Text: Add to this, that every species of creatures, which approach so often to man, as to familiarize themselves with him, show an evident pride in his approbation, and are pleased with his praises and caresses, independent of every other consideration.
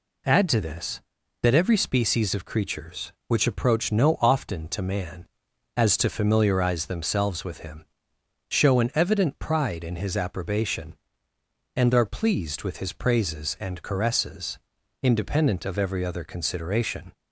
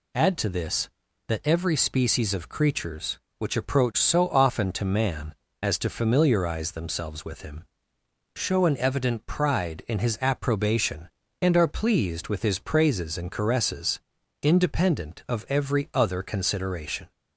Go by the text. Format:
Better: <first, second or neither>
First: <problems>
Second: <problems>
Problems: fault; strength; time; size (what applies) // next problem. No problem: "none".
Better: second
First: says "no" for "so"; at 3.9 s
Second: none